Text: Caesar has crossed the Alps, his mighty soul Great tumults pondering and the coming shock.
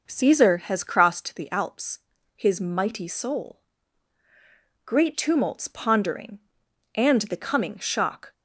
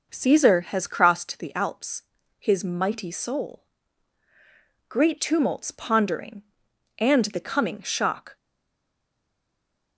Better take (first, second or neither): first